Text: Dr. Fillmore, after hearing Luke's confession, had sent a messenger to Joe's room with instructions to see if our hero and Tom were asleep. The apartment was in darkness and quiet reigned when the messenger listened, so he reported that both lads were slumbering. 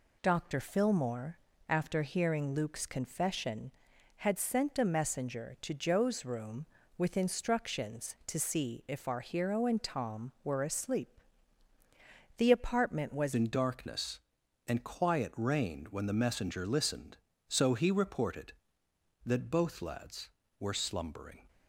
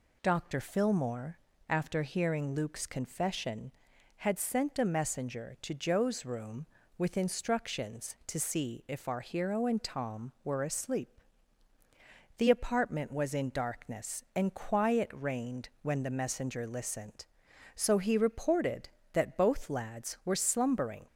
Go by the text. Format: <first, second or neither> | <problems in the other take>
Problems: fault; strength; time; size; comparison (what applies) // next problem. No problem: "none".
second | changes voice at "in"; from 13.3 s on; 8.1 s long